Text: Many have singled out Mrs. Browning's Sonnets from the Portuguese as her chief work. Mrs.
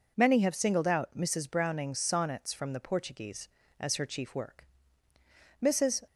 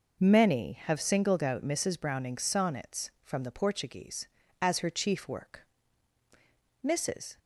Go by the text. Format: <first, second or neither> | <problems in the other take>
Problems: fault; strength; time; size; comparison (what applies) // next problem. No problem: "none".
neither | none